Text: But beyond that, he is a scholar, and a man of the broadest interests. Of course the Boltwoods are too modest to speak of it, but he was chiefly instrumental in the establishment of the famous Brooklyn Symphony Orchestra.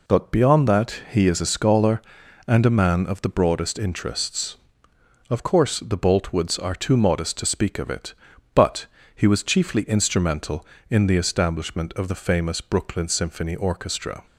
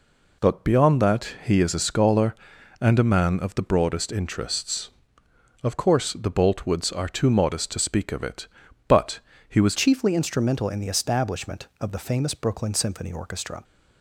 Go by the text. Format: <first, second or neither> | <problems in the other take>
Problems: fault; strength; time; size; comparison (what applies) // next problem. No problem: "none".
first | pauses between "but" and "he"; slight; at 9.1 s; 0.30 s long; slight in the first // changes voice at "chiefly"; from 9.7 s on; 3.9 s long